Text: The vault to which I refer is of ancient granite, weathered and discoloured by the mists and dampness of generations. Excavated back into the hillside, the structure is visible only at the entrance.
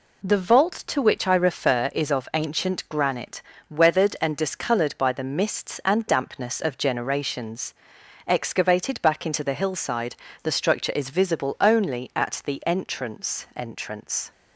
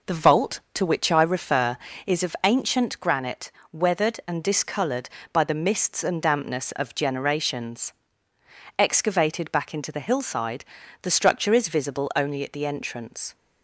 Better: second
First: says "entrance" twice; at 13.5 s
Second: none

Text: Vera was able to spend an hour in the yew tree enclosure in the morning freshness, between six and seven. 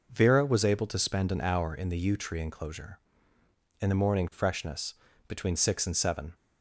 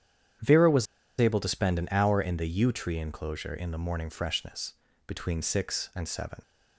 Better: first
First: none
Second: starts louder than the rest; strong; until 1.7 s; 9.5 dB // pauses between "was" and "able"; slight; at 0.8 s; 0.33 s long

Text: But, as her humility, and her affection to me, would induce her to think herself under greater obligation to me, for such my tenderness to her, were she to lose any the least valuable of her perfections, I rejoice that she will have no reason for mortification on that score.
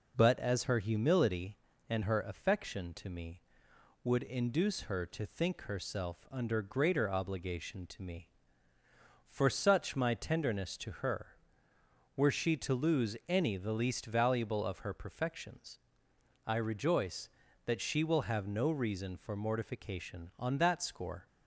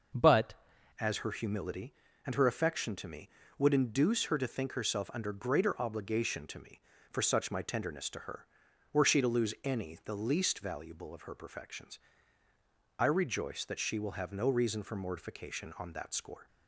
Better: first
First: none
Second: starts louder than the rest; noticeable; until 1.6 s; 6 dB // changes voice at "as"; from 1.0 s on; 15.4 s long

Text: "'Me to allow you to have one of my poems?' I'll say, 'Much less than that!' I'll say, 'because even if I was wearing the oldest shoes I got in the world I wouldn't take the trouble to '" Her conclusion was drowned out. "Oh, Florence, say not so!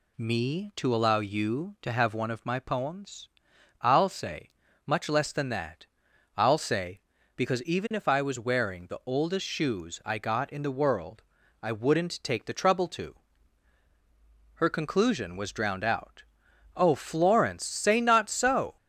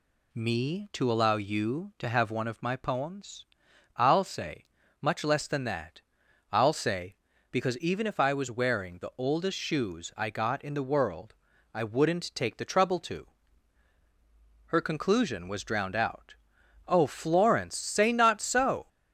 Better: neither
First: pauses between "world" and "I"; at 11.2 s; 0.40 s long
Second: pauses between "world" and "I"; at 11.3 s; 0.40 s long

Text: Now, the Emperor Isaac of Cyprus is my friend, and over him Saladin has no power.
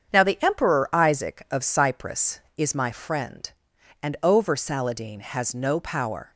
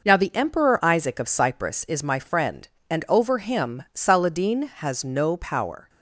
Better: second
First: starts louder than the rest; strong; until 1.1 s; 7.5 dB // skips "him"; at 4.5 s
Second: none

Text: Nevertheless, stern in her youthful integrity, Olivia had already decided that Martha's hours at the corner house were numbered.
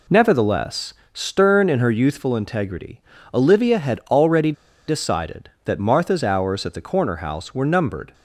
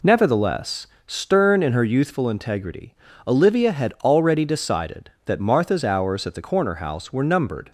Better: second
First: pauses between "already" and "decided"; slight; at 4.5 s; 0.35 s long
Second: none

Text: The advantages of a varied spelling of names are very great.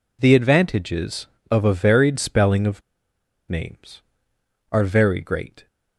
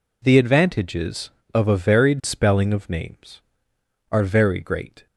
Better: second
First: pauses between "of" and "names"; noticeable; at 2.8 s; 0.69 s long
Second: none

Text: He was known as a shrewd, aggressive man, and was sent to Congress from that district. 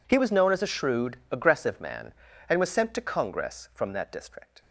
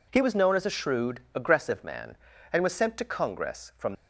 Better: first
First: none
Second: stops before "that district"; at 3.9 s

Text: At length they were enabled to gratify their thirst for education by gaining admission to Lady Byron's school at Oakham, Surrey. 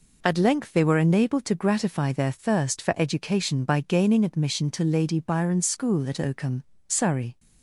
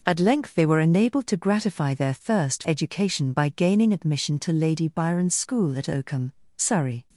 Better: first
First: none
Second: skips "for"; at 2.6 s

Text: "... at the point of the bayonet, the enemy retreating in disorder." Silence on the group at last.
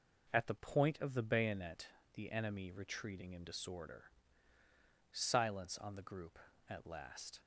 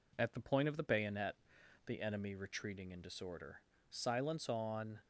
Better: first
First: none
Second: stops before "the group at last"; at 5.0 s

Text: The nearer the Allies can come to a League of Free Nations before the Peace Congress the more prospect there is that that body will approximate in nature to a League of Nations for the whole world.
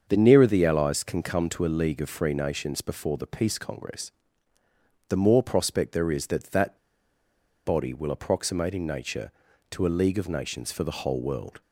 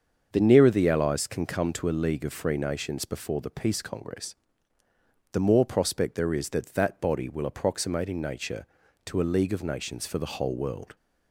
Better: second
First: starts louder than the rest; until 1.1 s; 7 dB // pauses between "Congress" and "the"; noticeable; at 4.1 s; 0.98 s long // pauses between "that" and "body"; noticeable; at 6.7 s; 0.88 s long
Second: starts louder than the rest; until 1.3 s; 7 dB // pauses between "Congress" and "the"; noticeable; at 4.3 s; 0.98 s long

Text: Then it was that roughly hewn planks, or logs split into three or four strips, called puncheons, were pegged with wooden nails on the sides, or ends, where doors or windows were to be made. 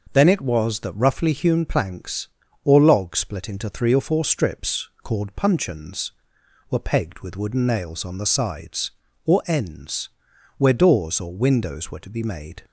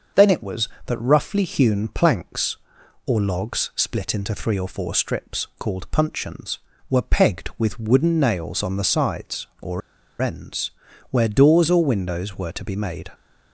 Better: first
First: none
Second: starts louder than the rest; until 1.3 s; 6.5 dB // pauses between "or" and "ends"; at 9.8 s; 0.41 s long

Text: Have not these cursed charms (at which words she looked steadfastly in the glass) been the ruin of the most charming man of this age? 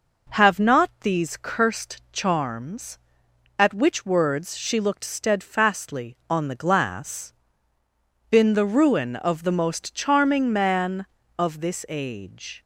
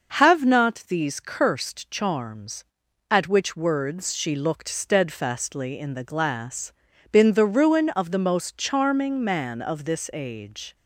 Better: second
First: says "on" for "in"; at 6.2 s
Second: none

